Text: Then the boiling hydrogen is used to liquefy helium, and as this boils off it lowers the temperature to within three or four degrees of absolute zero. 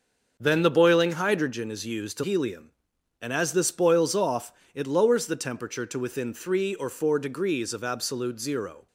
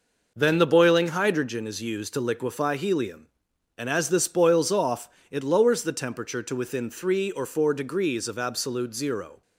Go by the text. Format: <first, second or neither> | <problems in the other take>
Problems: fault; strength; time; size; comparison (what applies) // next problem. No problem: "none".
second | starts louder than the rest; until 1.4 s; 6.5 dB // skips "liquefy"; at 2.2 s // pauses between "off" and "it"; slight; at 4.5 s; 0.22 s long; slight in the second